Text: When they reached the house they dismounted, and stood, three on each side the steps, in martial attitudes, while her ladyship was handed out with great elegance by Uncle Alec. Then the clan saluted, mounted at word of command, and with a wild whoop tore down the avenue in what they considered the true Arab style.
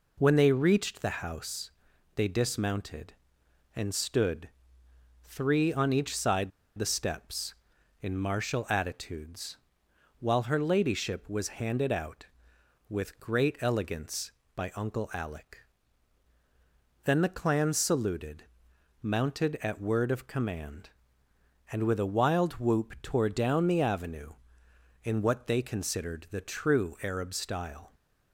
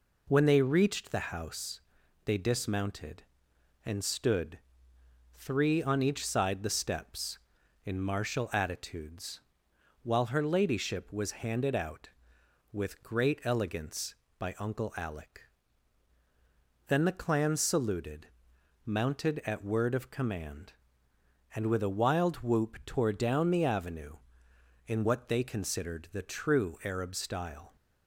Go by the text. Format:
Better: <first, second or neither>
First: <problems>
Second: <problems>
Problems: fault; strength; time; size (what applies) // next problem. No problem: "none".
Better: second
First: pauses between "house" and "they"; noticeable; at 1.7 s; 0.46 s long // pauses between "side" and "the"; slight; at 6.5 s; 0.27 s long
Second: pauses between "house" and "they"; noticeable; at 1.8 s; 0.46 s long